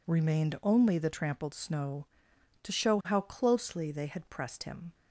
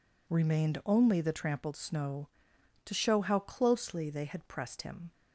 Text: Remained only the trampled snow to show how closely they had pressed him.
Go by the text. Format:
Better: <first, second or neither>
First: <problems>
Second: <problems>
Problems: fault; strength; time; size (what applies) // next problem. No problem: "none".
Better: neither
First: none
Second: none